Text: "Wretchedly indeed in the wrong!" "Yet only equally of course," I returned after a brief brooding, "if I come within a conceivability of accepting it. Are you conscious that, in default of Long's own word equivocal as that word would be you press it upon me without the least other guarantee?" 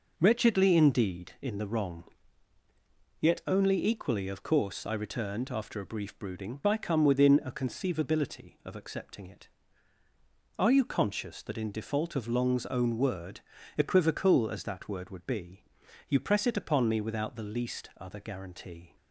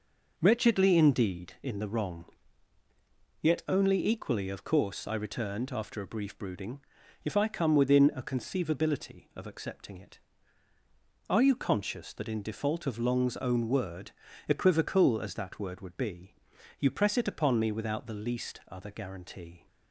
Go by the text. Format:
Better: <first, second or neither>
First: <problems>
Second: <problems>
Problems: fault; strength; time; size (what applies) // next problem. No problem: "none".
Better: second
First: skips "if"; at 6.6 s // pauses between "word" and "equivocal"; at 13.3 s; 0.38 s long // pauses between "be" and "you"; noticeable; at 15.6 s; 0.46 s long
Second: pauses between "word" and "equivocal"; at 14.1 s; 0.38 s long // pauses between "be" and "you"; noticeable; at 16.3 s; 0.46 s long